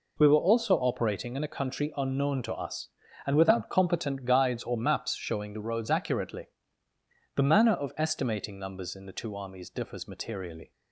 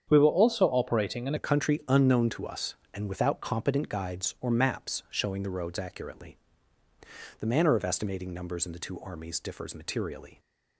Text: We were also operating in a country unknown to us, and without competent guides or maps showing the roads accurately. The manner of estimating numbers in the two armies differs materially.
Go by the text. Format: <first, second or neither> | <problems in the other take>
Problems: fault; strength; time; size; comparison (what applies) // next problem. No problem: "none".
first | starts louder than the rest; strong; until 1.0 s; 8 dB // changes voice at "a"; from 1.3 s on; 9.0 s long